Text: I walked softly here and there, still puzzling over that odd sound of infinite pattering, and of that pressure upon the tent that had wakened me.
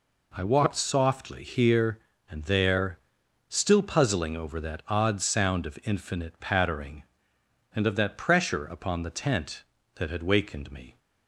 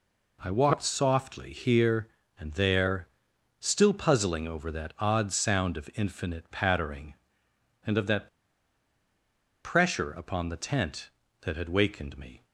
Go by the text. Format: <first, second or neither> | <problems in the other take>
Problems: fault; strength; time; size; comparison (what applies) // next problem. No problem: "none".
first | pauses between "that" and "pressure"; strong; at 8.2 s; 1.3 s long